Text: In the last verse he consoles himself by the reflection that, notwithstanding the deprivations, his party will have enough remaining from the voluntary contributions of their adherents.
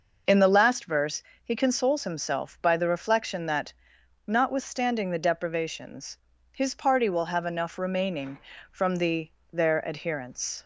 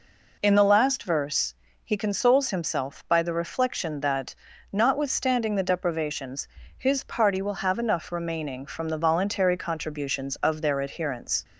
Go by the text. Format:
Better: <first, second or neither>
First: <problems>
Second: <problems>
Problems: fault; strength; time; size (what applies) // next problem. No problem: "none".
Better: second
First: pauses between "verse" and "he"; slight; at 1.2 s; 0.22 s long // skips "voluntary contributions of"; at 9.4 s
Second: pauses between "verse" and "he"; slight; at 1.5 s; 0.32 s long